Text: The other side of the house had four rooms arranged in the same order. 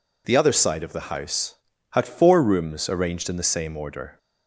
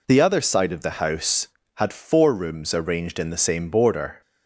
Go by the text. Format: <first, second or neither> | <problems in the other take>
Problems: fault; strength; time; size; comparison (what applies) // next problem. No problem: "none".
first | says "border" for "order"; at 3.6 s